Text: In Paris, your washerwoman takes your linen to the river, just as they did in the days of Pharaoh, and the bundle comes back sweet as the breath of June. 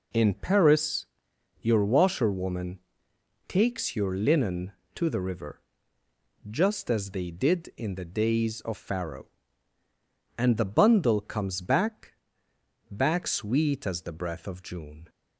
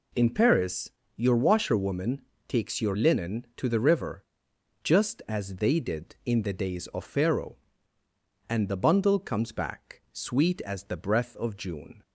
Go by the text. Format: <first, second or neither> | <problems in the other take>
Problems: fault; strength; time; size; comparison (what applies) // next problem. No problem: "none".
second | pauses between "washerwoman" and "takes"; noticeable; at 2.7 s; 0.66 s long; slight in the second // says "back" twice; at 12.8 s